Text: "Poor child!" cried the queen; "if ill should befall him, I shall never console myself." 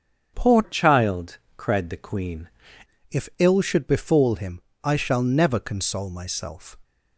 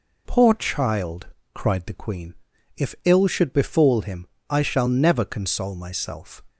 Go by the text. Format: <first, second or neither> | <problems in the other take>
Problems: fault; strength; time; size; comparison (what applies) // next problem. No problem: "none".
second | starts louder than the rest; strong; until 1.3 s; 7.5 dB // changes voice from "child" to "queen"; from 0.6 to 2.4 s; 1.8 s long